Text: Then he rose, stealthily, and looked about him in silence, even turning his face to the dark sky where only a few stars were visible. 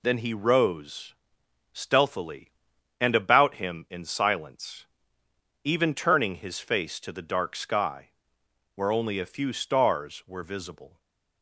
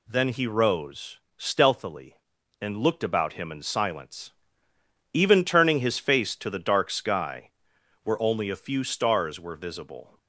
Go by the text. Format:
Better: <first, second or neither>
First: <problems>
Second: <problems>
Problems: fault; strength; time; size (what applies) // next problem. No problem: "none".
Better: second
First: skips "looked"; at 3.1 s // pauses between "sky" and "where"; noticeable; at 8.0 s; 0.68 s long // stays silent after the last word; slight; from 10.8 s on; 0.6 s long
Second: pauses between "sky" and "where"; noticeable; at 7.4 s; 0.54 s long